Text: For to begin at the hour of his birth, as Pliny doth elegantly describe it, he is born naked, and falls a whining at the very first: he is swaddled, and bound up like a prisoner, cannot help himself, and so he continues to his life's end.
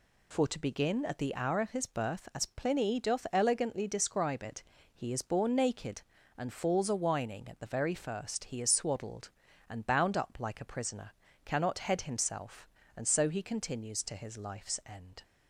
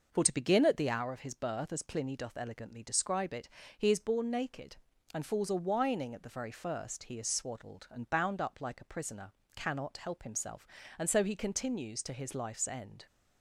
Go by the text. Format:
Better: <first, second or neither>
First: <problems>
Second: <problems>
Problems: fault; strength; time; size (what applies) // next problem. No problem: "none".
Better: second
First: says "head" for "help"; at 11.7 s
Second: none